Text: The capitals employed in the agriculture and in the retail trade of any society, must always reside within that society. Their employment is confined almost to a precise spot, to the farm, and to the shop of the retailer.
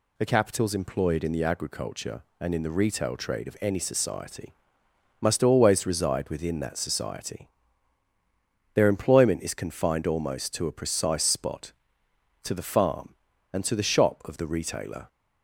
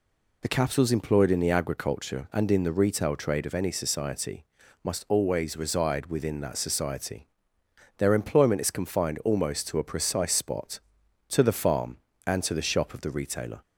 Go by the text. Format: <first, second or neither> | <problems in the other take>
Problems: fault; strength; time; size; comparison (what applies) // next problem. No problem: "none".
neither | none